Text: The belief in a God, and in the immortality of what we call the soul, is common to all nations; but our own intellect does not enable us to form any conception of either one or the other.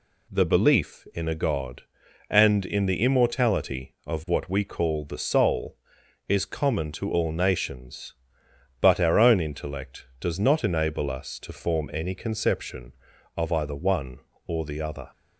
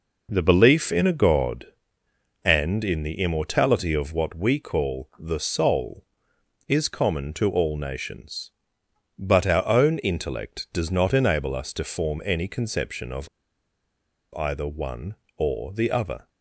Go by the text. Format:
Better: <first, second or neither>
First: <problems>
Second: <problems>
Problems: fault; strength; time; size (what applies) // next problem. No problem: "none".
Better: first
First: none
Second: pauses between "of" and "either"; at 13.2 s; 1.0 s long